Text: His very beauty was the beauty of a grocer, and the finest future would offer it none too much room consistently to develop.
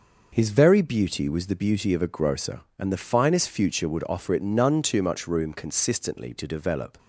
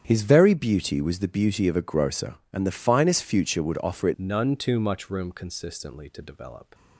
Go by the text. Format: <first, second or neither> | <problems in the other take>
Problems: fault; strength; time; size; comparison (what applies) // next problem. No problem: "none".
first | starts louder than the rest; strong; until 1.0 s; 8.5 dB // changes voice at "none"; from 4.1 s on; 2.6 s long